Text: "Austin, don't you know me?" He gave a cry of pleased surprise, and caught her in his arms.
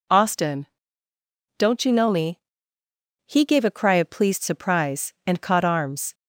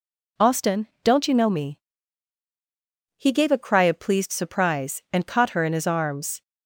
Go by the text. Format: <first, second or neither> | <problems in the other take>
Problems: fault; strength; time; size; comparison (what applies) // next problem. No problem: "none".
second | skips "her in his"; at 5.6 s